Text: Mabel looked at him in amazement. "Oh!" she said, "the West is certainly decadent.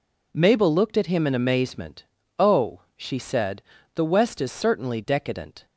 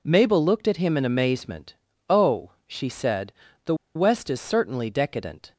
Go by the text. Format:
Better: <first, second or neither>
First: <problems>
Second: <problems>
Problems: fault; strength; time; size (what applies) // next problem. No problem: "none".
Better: first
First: none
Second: pauses between "the" and "West"; slight; at 3.7 s; 0.21 s long